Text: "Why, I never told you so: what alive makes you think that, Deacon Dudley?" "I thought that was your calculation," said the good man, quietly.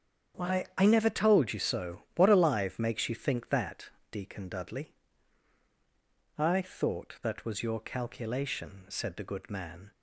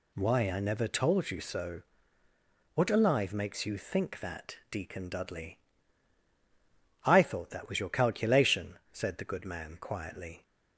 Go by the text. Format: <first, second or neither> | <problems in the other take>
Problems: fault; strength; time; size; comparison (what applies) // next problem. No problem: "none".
second | starts louder than the rest; strong; until 1.4 s; 8 dB // stops before "quietly"; at 9.9 s